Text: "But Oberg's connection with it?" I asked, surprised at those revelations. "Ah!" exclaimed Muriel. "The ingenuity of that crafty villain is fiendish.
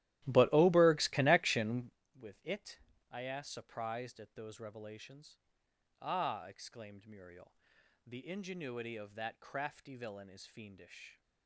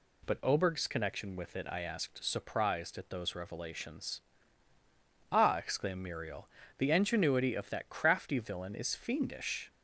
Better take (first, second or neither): second